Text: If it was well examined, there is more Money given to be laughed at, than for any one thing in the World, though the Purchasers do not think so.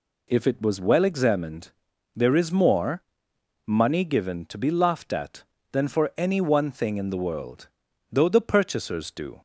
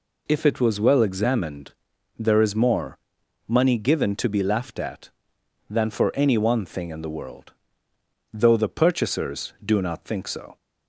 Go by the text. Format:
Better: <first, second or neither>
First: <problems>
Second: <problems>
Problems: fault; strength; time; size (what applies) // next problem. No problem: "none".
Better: second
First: pauses between "more" and "Money"; noticeable; at 3.0 s; 0.62 s long // stops before "not think so"; at 9.3 s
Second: pauses between "more" and "Money"; noticeable; at 2.9 s; 0.50 s long